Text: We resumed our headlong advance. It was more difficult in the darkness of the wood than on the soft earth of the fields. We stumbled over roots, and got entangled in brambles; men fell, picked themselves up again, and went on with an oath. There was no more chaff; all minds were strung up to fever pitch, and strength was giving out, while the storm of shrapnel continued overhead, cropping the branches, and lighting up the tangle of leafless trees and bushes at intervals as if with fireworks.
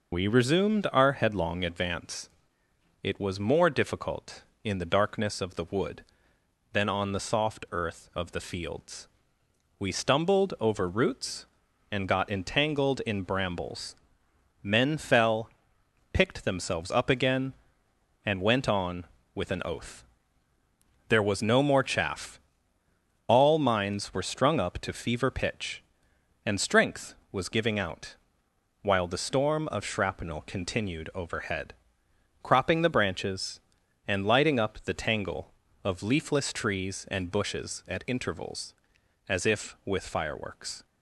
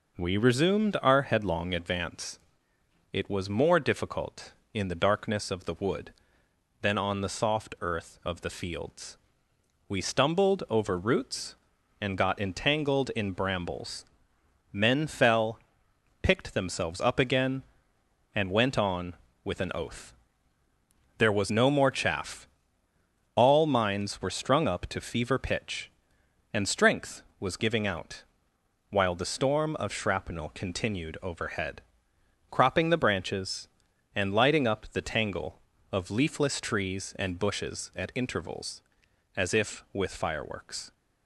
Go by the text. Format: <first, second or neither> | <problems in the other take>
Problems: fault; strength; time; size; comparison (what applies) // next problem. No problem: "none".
second | loses the start of "We"; at 0.1 s; 60 ms